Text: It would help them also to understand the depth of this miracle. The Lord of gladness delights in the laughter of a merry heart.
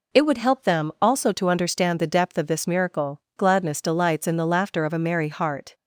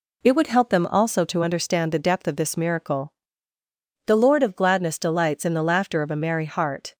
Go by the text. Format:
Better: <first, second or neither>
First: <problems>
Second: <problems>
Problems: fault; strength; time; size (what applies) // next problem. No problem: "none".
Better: second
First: skips "The Lord of"; at 3.2 s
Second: none